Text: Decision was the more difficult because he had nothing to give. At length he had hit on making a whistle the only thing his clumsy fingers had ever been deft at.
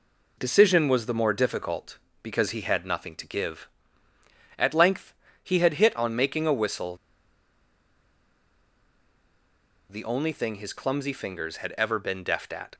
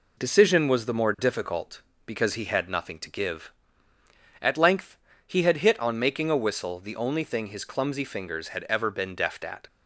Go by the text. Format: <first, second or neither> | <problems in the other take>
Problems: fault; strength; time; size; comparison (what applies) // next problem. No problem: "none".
second | pauses between "length" and "he"; slight; at 5.1 s; 0.30 s long; slight in the second // pauses between "whistle" and "the"; strong; at 6.9 s; 2.9 s long